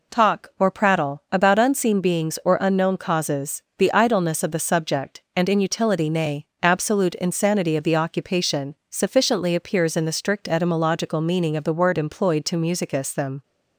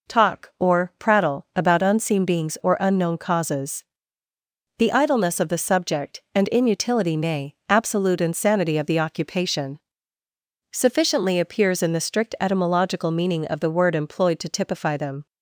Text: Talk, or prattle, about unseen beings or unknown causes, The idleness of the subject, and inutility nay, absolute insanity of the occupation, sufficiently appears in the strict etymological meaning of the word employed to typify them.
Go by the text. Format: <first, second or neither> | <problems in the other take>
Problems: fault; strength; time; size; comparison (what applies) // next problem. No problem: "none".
second | says "musicus" for "typify"; at 12.5 s